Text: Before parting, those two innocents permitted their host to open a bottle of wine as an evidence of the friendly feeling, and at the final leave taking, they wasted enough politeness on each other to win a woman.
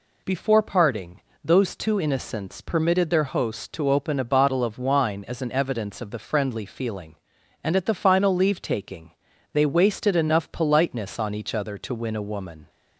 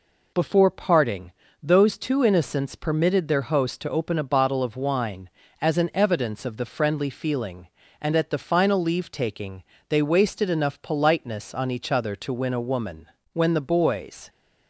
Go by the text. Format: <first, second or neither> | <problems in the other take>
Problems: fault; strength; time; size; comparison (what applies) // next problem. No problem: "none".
first | goes on to say "When the boys"; noticeable; from 13.3 s on; 0.96 s long